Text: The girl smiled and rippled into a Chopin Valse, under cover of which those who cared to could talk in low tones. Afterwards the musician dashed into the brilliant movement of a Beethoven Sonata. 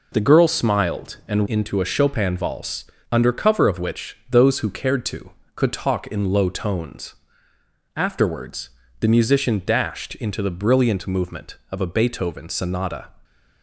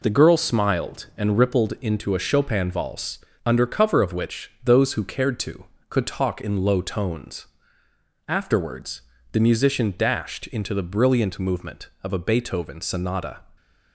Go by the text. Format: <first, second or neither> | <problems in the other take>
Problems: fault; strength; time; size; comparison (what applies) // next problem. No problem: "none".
second | skips "rippled"; at 1.4 s // pauses between "Afterwards" and "the"; slight; at 8.7 s; 0.30 s long; slight in the second